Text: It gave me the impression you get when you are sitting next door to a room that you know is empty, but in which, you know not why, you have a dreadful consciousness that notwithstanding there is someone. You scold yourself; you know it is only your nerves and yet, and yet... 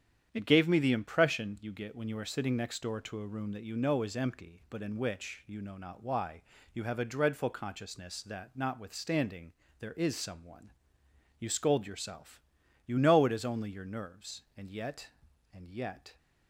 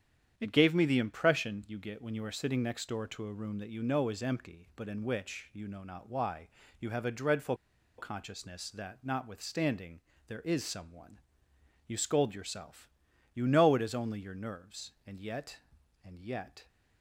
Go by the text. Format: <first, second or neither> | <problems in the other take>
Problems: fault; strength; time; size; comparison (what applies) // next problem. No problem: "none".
first | starts louder than the rest; strong; until 1.3 s; 9 dB; strong in the first // pauses between "dreadful" and "consciousness"; at 7.5 s; 0.42 s long // pauses between "notwithstanding" and "there"; slight; at 10.0 s; 0.26 s long; slight in the first